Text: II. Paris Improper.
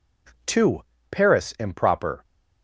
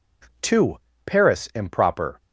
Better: neither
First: none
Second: none

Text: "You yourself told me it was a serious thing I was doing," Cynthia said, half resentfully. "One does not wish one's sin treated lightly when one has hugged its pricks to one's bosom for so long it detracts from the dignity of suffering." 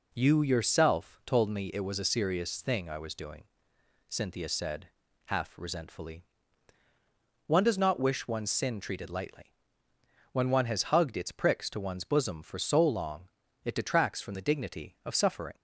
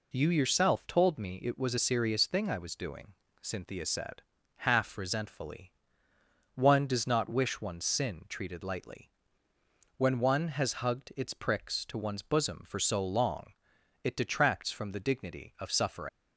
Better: first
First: pauses between "lightly" and "when"; noticeable; at 9.5 s; 0.78 s long // pauses between "long" and "it"; slight; at 13.2 s; 0.34 s long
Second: pauses between "lightly" and "when"; noticeable; at 9.1 s; 0.88 s long // pauses between "long" and "it"; noticeable; at 13.5 s; 0.50 s long // leaves "suffering" unfinished; at 16.0 s; 135 ms

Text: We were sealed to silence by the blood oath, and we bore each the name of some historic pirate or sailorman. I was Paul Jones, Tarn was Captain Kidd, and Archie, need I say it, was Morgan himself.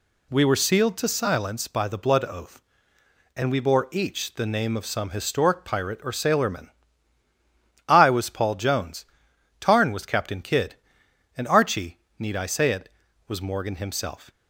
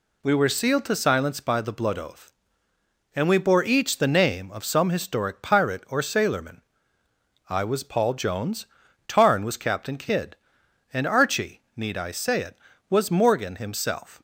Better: neither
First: none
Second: none

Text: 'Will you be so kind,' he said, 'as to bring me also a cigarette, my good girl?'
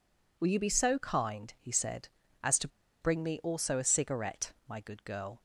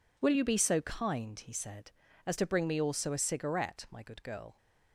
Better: second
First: pauses between "to" and "bring"; slight; at 2.6 s; 0.33 s long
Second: none

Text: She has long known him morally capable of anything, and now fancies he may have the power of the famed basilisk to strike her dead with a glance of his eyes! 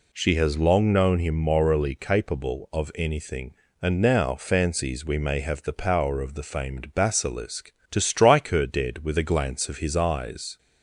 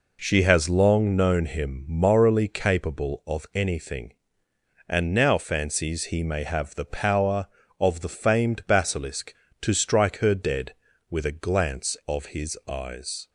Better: second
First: says "we" for "he"; at 5.0 s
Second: none

